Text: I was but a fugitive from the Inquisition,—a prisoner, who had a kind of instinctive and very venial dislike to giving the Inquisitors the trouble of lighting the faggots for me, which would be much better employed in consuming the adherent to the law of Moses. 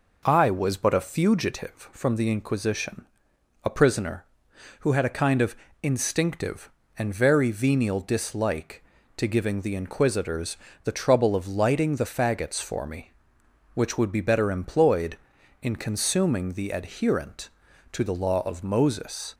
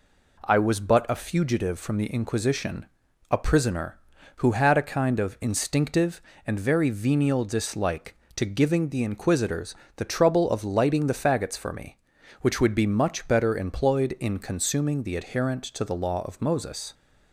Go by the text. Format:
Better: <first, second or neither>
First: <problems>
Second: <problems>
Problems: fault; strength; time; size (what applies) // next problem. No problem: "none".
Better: second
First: pauses between "of" and "instinctive"; slight; at 5.5 s; 0.28 s long // pauses between "Inquisitors" and "the"; slight; at 10.5 s; 0.28 s long // skips "much"; at 14.2 s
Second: pauses between "Inquisitors" and "the"; slight; at 9.7 s; 0.22 s long